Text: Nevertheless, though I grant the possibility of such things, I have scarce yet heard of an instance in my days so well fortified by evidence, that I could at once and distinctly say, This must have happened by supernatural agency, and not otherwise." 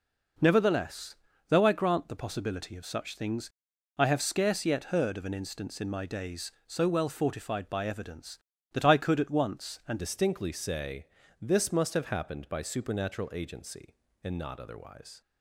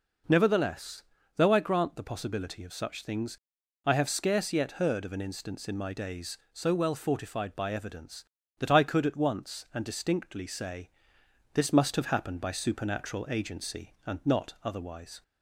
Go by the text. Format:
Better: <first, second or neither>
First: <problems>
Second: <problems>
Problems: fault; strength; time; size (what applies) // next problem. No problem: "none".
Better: second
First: changes voice at "distinctly"; from 9.9 s on; 5.3 s long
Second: none